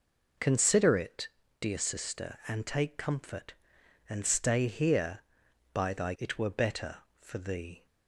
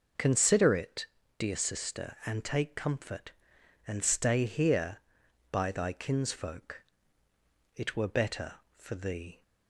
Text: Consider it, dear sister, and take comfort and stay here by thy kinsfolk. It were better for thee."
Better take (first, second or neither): second